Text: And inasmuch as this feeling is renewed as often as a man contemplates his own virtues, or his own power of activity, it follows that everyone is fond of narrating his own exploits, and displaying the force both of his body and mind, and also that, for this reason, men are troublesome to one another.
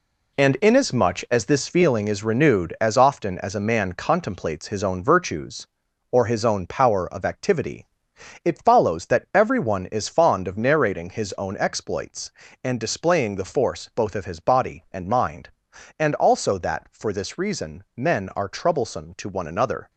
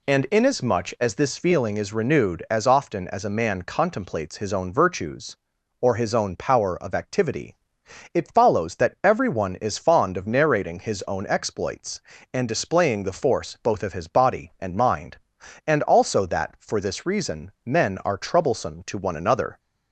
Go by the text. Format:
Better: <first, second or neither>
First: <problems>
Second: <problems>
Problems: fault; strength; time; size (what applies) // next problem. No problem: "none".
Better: second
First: gets quieter; strong; throughout; 8 dB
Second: none